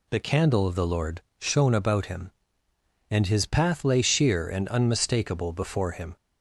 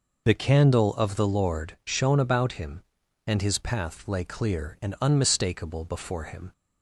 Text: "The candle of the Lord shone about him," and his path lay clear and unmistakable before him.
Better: second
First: pauses between "Lord" and "shone"; slight; at 1.1 s; 0.18 s long // says "sheer" for "clear"; at 3.9 s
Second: none

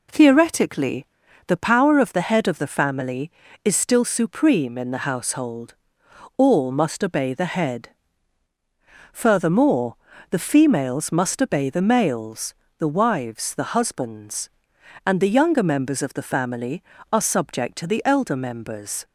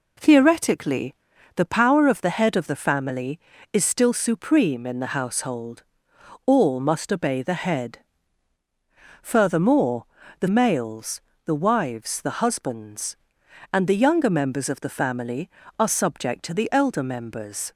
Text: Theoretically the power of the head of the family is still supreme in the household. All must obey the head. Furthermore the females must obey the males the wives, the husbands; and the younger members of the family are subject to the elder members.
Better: first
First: pauses between "Theoretically" and "the"; at 1.0 s; 0.40 s long // pauses between "Furthermore" and "the"; slight; at 9.9 s; 0.36 s long // pauses between "males" and "the"; slight; at 12.5 s; 0.26 s long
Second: pauses between "Theoretically" and "the"; at 1.1 s; 0.40 s long // pauses between "Furthermore" and "the"; slight; at 10.0 s; 0.36 s long // skips "females must obey the"; at 10.4 s // pauses between "males" and "the"; slight; at 11.1 s; 0.26 s long

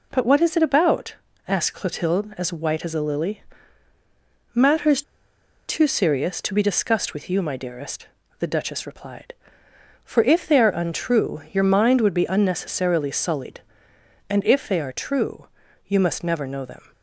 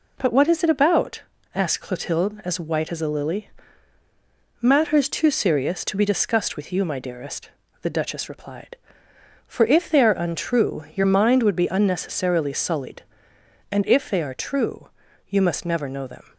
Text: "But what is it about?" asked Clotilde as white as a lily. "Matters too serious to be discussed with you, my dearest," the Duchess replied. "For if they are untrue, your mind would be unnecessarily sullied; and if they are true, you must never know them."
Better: second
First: pauses between "Matters" and "too"; noticeable; at 5.0 s; 0.66 s long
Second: none

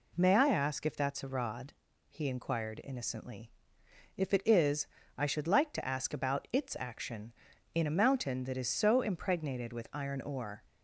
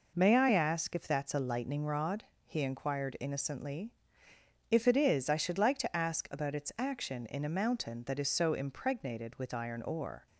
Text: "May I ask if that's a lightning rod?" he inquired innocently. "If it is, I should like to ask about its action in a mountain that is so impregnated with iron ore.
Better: second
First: skips "lightning"; at 1.2 s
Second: none

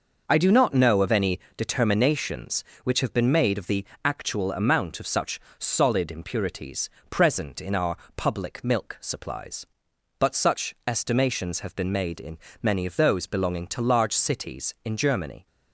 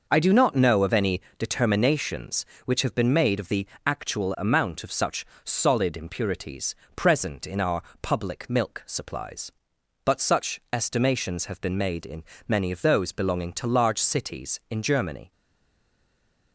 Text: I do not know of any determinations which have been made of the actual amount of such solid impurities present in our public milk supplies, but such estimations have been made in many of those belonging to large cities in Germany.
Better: first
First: pauses between "any" and "determinations"; slight; at 1.3 s; 0.18 s long // pauses between "the" and "actual"; slight; at 3.8 s; 0.20 s long // pauses between "such" and "solid"; slight; at 5.3 s; 0.20 s long // pauses between "impurities" and "present"; slight; at 6.8 s; 0.22 s long // pauses between "our" and "public"; slight; at 7.9 s; 0.18 s long // pauses between "in" and "many"; slight; at 12.3 s; 0.24 s long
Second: pauses between "any" and "determinations"; slight; at 1.1 s; 0.18 s long // pauses between "the" and "actual"; slight; at 3.6 s; 0.20 s long // pauses between "such" and "solid"; slight; at 5.2 s; 0.20 s long // pauses between "impurities" and "present"; slight; at 6.7 s; 0.22 s long // pauses between "our" and "public"; slight; at 7.8 s; 0.18 s long // pauses between "in" and "many"; slight; at 12.2 s; 0.24 s long // stays silent after the last word; noticeable; from 15.3 s on; 1.2 s long

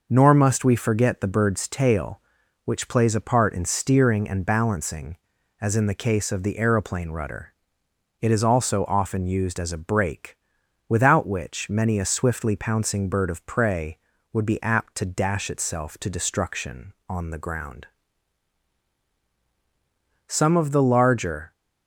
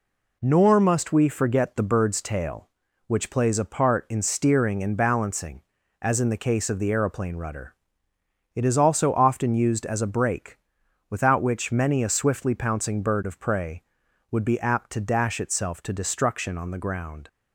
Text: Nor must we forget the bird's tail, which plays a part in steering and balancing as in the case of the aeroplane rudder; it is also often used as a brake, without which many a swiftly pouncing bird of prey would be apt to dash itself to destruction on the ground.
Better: second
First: goes on to say "Some of the larger"; noticeable; from 20.2 s on; 1.2 s long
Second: none

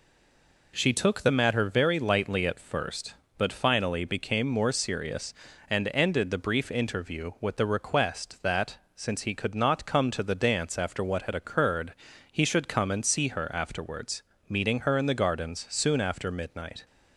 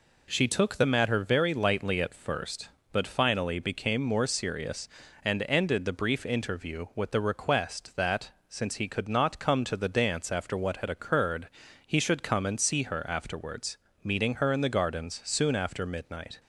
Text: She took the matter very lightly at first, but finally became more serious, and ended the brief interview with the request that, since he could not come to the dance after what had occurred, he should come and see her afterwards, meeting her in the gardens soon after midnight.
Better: second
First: stays silent before the first word; slight; until 0.7 s; 0.7 s long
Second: none

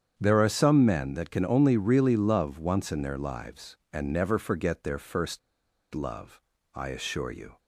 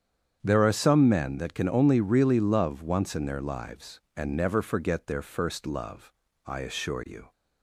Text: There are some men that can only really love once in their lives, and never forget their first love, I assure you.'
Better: second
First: starts louder than the rest; strong; until 1.1 s; 8 dB // pauses between "first" and "love"; noticeable; at 5.3 s; 0.55 s long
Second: starts louder than the rest; strong; until 1.4 s; 8 dB

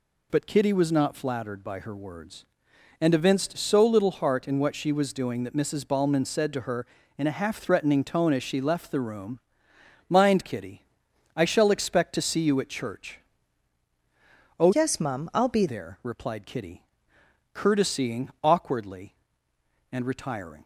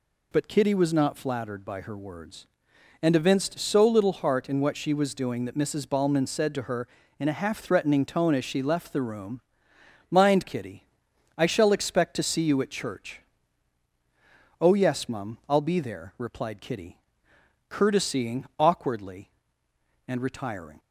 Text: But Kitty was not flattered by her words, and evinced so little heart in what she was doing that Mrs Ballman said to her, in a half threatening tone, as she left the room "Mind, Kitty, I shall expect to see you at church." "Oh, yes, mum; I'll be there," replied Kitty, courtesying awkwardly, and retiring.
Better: second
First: pauses between "room" and "Mind"; noticeable; at 9.4 s; 0.68 s long // changes voice from "yes" to "be"; from 14.7 to 15.6 s; 0.9 s long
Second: pauses between "room" and "Mind"; noticeable; at 9.4 s; 0.68 s long

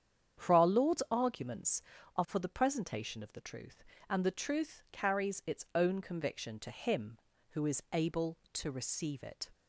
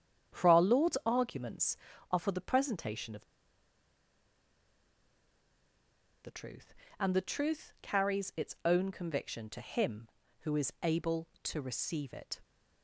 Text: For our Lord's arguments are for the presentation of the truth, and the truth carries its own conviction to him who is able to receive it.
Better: first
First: starts louder than the rest; strong; until 1.4 s; 8 dB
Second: starts louder than the rest; strong; until 1.4 s; 8 dB // pauses between "of" and "the"; strong; at 3.2 s; 2.9 s long

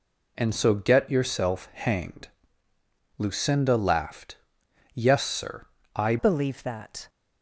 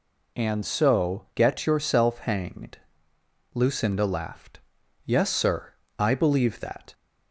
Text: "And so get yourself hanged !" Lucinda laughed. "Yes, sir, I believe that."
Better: second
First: changes voice at "believe"; from 6.1 s on; 0.9 s long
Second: none

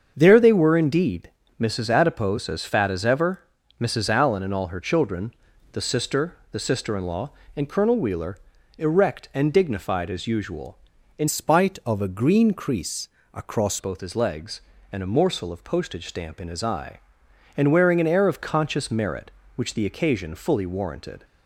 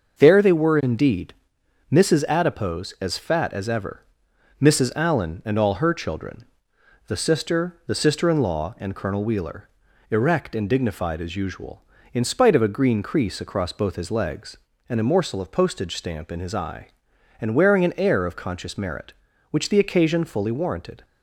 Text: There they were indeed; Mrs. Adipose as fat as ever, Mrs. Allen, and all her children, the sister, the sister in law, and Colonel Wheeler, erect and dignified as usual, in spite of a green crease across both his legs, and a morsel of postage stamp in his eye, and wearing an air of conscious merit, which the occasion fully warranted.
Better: second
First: starts louder than the rest; until 1.1 s; 7 dB // changes voice from "spite" to "across"; from 11.2 to 13.8 s; 2.6 s long // pauses between "crease" and "across"; slight; at 13.0 s; 0.26 s long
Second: starts louder than the rest; until 1.2 s; 6.5 dB

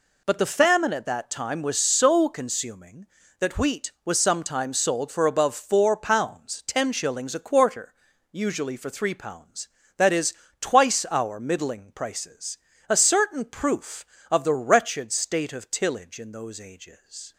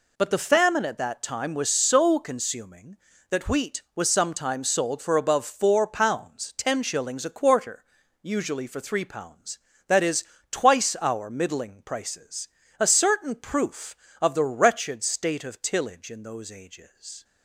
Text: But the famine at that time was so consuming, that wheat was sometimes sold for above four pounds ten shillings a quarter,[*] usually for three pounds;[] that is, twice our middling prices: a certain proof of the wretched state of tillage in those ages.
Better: neither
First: none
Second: none

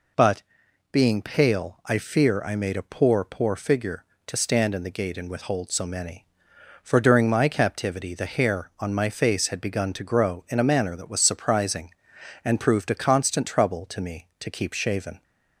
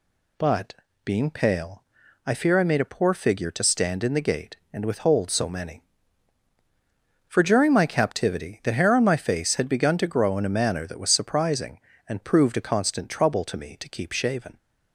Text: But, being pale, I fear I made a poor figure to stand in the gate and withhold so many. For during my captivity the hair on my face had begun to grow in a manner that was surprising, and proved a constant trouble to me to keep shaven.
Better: second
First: says "poor" twice; at 3.2 s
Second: none

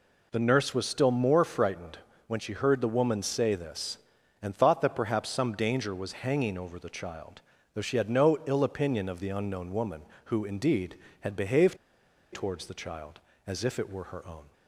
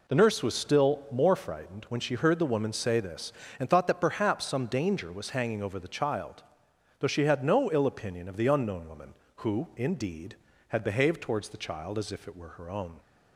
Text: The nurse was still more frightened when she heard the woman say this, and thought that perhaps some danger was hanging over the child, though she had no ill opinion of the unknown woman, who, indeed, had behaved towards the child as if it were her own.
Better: second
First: pauses between "frightened" and "when"; slight; at 1.9 s; 0.28 s long // pauses between "behaved" and "towards"; noticeable; at 11.7 s; 0.57 s long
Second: none

